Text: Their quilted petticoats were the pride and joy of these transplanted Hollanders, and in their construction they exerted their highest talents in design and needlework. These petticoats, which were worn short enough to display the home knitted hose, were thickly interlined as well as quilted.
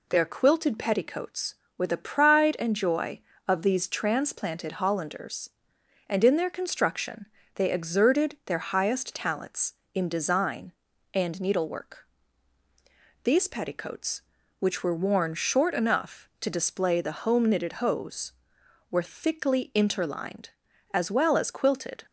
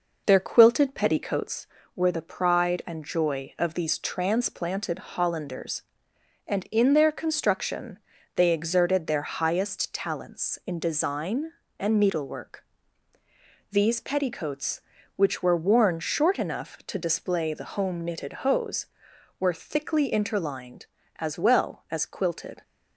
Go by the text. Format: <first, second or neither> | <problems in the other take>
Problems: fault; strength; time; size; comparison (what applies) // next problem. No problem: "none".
first | starts louder than the rest; noticeable; until 1.6 s; 5 dB // pauses between "construction" and "they"; slight; at 7.9 s; 0.36 s long; slight in the first